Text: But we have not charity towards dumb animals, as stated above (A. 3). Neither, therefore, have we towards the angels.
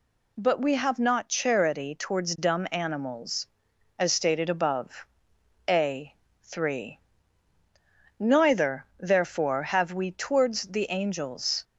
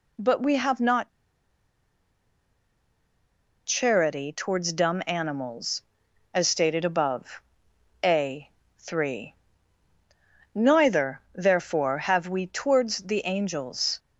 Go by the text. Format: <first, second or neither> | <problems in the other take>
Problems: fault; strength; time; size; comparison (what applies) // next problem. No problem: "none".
first | pauses between "not" and "charity"; strong; at 1.0 s; 2.5 s long